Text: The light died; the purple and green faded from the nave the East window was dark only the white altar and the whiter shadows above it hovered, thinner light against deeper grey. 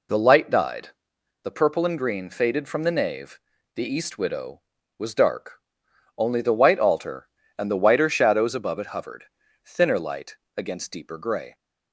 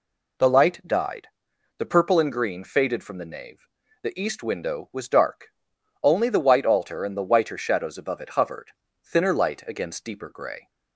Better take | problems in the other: second | pauses between "nave" and "the"; at 3.3 s; 0.38 s long; slight in the second // says "widow" for "window"; at 4.1 s // pauses between "dark" and "only"; noticeable; at 5.6 s; 0.58 s long; noticeable in the second // pauses between "light" and "against"; slight; at 10.3 s; 0.24 s long

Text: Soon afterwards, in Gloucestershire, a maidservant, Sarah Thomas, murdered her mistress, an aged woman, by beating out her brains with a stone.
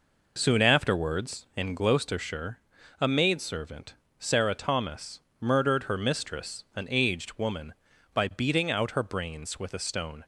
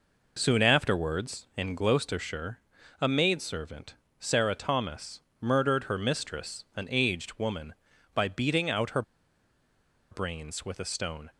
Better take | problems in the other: first | pauses between "her" and "brains"; at 9.0 s; 1.0 s long

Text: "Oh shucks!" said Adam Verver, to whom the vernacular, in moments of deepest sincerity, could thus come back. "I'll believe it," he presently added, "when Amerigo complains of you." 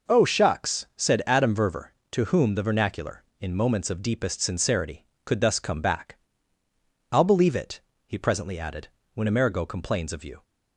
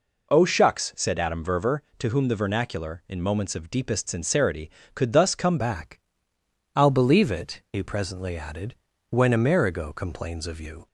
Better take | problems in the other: first | changes voice at "back"; from 5.5 s on; 5.3 s long

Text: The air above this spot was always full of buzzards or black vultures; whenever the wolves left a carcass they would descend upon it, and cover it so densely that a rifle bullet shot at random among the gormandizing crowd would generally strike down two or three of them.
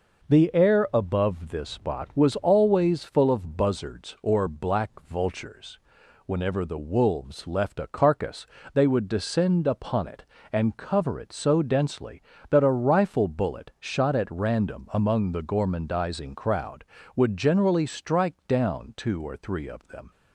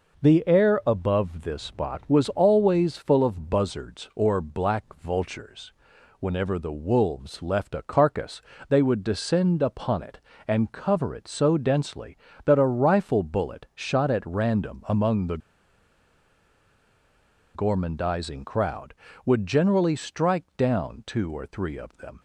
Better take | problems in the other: first | pauses between "carcass" and "they"; slight; at 8.3 s; 0.30 s long; slight in the first // pauses between "the" and "gormandizing"; strong; at 15.3 s; 2.1 s long

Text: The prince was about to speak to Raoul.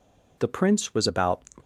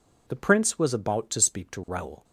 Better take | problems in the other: second | stops before "to speak to Raoul"; at 1.6 s

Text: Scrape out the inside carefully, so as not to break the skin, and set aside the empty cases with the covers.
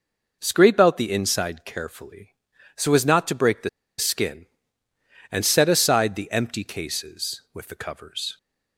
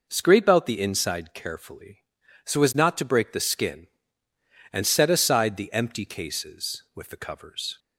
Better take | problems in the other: second | pauses between "the" and "skin"; slight; at 3.6 s; 0.29 s long

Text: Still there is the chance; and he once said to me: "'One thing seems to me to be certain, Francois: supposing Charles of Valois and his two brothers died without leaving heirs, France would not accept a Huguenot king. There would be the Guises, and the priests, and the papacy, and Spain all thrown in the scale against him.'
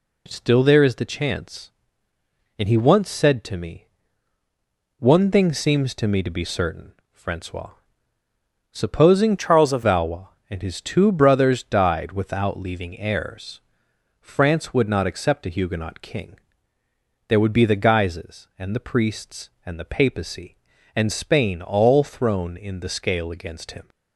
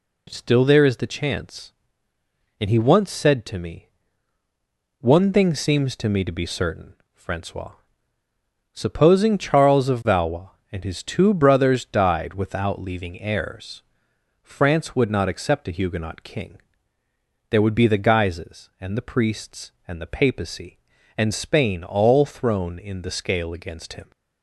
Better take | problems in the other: second | changes voice from "Charles" to "of"; from 9.3 to 9.8 s; 0.5 s long

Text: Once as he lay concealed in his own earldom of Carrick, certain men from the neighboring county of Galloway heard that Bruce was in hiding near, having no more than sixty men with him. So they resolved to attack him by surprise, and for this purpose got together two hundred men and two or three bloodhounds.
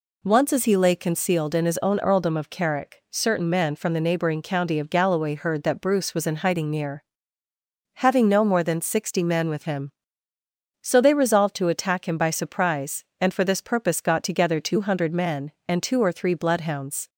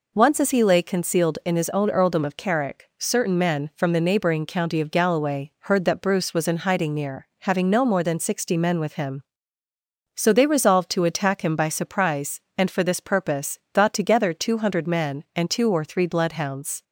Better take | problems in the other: neither | none

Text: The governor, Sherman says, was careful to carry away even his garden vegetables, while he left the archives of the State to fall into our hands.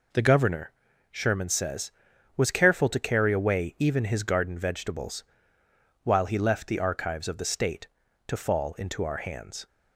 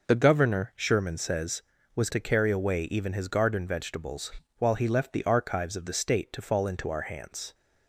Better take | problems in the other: first | skips "careful"; at 2.0 s

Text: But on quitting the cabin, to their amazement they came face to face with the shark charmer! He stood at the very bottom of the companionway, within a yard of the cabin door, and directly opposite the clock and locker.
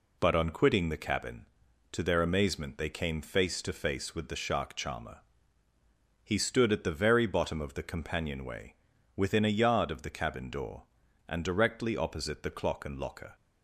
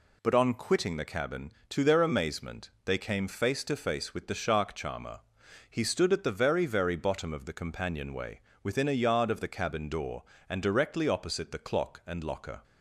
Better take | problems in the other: first | says "very" twice; at 6.6 s

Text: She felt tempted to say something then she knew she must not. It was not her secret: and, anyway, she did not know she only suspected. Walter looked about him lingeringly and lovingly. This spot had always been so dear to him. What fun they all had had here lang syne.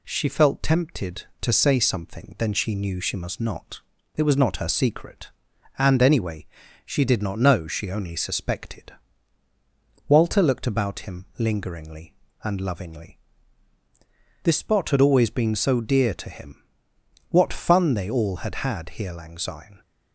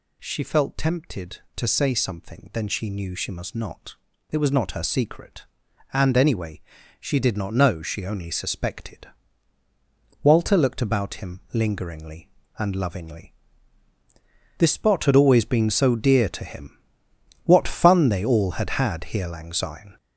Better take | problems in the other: first | gets louder; noticeable; throughout; 5.5 dB

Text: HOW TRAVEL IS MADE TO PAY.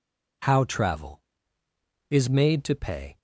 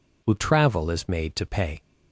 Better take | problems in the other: first | says "Who" for "HOW"; at 0.2 s

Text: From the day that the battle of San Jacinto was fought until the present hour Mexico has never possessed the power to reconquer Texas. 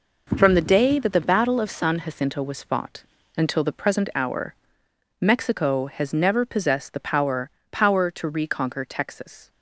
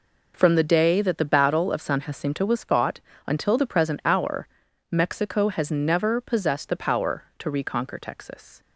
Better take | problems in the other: second | pauses between "fought" and "until"; slight; at 3.0 s; 0.34 s long; slight in the second // pauses between "hour" and "Mexico"; noticeable; at 4.5 s; 0.66 s long; also in the second // says "power" twice; at 7.7 s

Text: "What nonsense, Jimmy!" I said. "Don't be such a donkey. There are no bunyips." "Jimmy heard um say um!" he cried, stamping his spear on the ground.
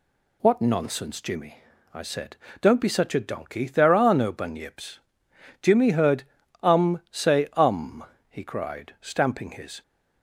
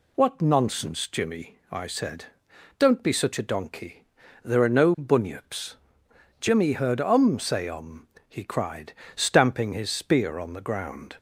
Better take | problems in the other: second | pauses between "heard" and "um"; at 6.2 s; 0.40 s long // stops before "spear on the ground"; at 9.8 s

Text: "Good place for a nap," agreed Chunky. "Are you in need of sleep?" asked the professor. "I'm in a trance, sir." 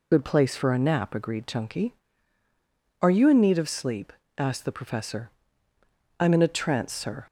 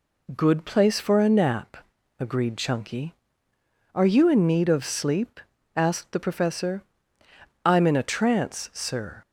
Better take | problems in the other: second | loses the start of "Good"; at 0.1 s; 45 ms

